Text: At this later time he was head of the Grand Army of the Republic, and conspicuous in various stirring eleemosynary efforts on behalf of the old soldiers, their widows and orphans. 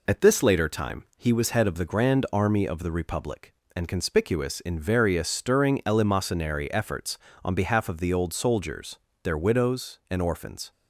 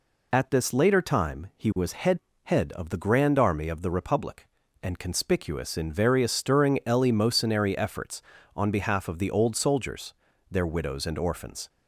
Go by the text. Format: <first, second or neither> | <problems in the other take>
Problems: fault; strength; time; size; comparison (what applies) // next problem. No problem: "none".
first | says "head" twice; at 2.4 s